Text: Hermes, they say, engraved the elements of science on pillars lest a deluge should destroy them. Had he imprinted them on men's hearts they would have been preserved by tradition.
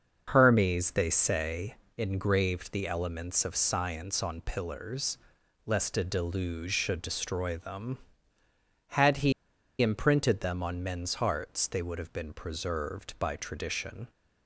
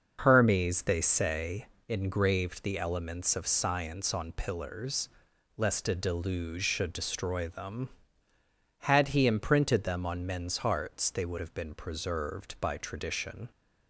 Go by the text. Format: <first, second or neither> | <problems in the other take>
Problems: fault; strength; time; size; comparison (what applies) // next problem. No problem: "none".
second | starts louder than the rest; noticeable; until 1.3 s; 6 dB // pauses between "pillars" and "lest"; noticeable; at 5.1 s; 0.48 s long; noticeable in the second // pauses between "he" and "imprinted"; noticeable; at 9.3 s; 0.48 s long